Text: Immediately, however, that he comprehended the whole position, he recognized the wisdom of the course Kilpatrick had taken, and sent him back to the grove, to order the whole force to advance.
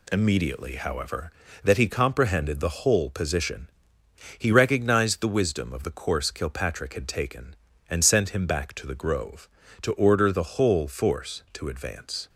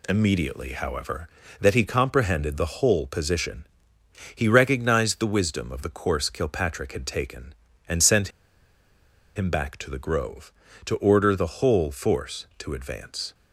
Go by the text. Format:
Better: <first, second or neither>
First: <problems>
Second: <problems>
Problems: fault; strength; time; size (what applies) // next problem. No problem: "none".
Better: first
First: none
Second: pauses between "sent" and "him"; at 8.2 s; 1.0 s long